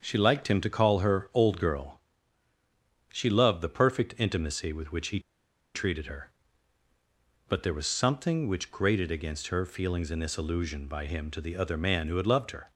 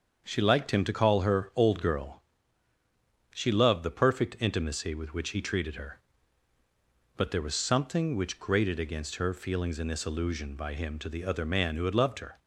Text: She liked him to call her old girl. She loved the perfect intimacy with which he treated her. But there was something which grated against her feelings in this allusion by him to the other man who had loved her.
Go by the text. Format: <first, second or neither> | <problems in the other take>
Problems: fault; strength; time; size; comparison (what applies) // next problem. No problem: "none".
second | starts louder than the rest; until 1.0 s; 6.5 dB; also in the second // pauses between "he" and "treated"; noticeable; at 5.1 s; 0.55 s long